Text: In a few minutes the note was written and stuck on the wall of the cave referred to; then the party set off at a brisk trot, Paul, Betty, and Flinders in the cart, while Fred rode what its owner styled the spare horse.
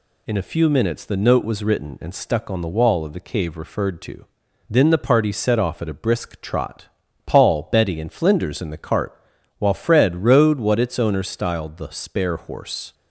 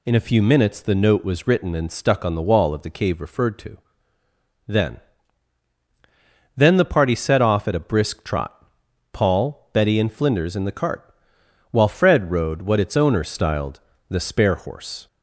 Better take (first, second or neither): first